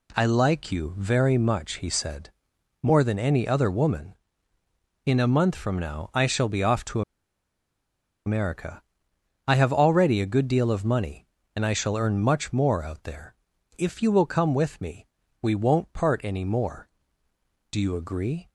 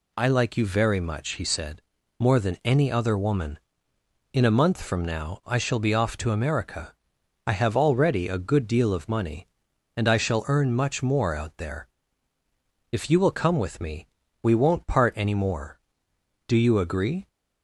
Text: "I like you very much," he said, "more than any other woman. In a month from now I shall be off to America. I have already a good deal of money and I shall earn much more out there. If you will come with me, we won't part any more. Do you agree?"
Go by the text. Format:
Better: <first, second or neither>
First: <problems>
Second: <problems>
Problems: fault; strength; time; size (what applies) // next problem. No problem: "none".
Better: second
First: pauses between "to" and "America"; strong; at 7.0 s; 1.2 s long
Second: none